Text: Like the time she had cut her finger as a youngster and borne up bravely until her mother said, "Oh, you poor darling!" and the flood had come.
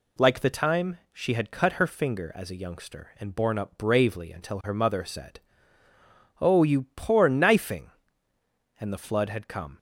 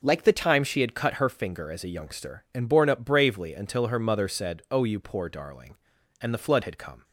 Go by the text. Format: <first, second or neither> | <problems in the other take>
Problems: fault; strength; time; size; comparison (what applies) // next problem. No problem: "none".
second | pauses between "time" and "she"; slight; at 0.9 s; 0.16 s long // says "knifing" for "darling"; at 7.2 s